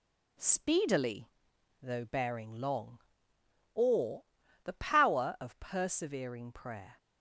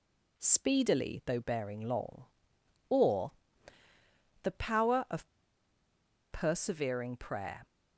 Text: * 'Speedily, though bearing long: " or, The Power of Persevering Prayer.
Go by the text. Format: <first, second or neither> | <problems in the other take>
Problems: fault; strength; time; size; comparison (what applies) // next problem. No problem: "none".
first | pauses between "of" and "Persevering"; at 5.2 s; 1.0 s long